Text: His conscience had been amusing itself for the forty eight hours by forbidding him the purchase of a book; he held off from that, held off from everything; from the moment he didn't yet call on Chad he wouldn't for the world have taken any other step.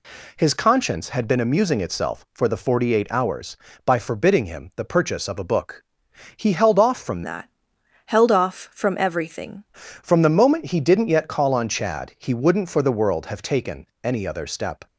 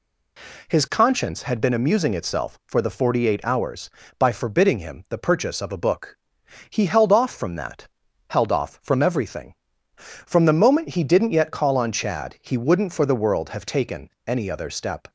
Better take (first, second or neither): second